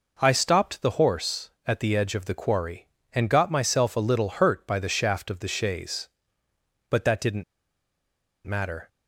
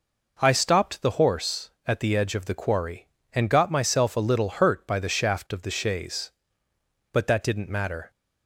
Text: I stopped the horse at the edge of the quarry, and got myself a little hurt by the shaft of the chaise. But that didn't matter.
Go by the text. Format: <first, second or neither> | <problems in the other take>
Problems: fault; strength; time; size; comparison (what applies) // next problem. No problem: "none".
second | pauses between "didn't" and "matter"; at 7.4 s; 1.0 s long